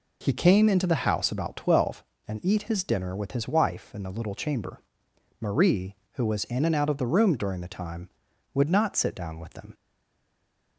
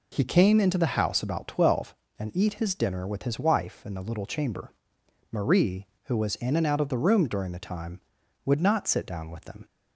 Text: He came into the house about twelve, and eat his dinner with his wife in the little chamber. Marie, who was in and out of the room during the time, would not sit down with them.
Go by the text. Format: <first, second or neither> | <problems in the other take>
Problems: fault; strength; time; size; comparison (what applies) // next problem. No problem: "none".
second | stays silent after the last word; from 9.7 s on; 1.0 s long